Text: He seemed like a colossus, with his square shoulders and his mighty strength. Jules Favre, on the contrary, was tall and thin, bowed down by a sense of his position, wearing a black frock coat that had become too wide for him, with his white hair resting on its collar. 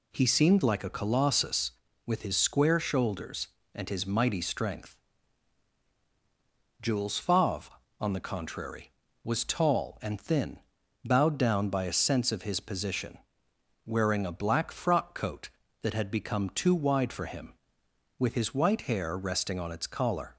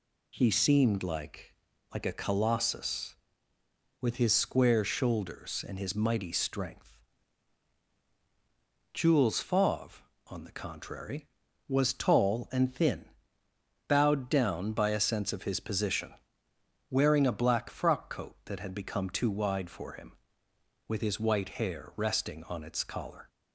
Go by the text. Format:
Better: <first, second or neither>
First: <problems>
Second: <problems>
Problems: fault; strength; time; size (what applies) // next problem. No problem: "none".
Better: first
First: none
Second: says "like" twice; at 1.9 s